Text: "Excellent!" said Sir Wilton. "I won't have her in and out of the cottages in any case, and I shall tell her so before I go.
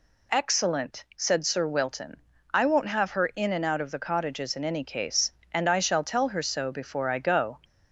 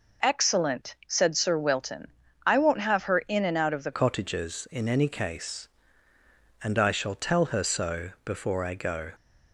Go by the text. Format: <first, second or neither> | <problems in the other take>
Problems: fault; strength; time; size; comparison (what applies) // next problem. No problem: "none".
first | changes voice at "cottages"; from 3.9 s on; 5.2 s long